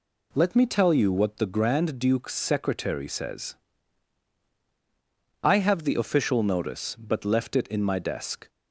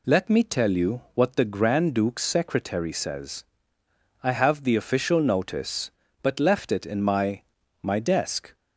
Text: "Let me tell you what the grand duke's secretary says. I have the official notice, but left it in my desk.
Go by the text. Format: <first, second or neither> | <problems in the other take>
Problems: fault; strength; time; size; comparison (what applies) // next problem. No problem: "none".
first | says "my" twice; at 7.8 s